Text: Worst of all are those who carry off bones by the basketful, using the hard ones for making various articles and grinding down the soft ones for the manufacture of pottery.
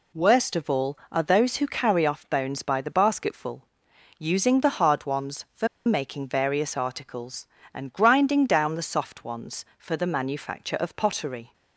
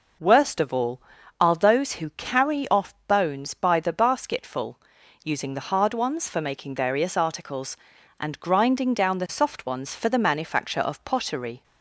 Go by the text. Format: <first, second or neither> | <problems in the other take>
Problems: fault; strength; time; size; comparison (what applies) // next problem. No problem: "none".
second | pauses between "for" and "making"; slight; at 5.6 s; 0.19 s long